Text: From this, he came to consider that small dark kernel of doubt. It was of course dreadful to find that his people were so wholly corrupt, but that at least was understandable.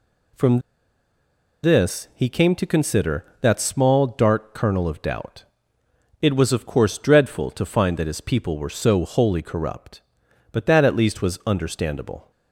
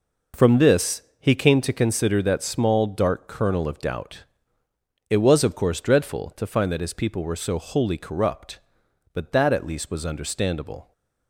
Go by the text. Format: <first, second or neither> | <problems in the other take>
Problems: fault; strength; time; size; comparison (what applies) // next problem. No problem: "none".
second | pauses between "From" and "this"; at 0.5 s; 1.0 s long